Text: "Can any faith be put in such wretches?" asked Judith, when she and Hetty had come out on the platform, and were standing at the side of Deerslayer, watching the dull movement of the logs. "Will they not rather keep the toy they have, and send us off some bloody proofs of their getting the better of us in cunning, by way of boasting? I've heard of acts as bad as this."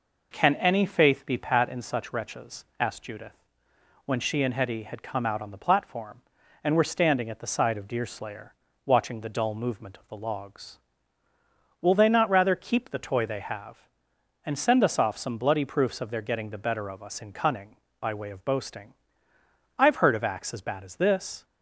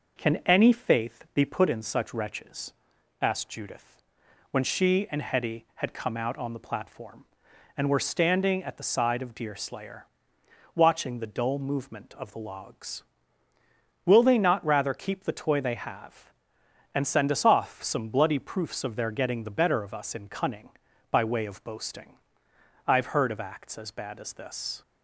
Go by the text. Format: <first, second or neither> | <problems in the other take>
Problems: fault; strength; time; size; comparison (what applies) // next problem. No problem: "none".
second | says "pat" for "put"; at 1.3 s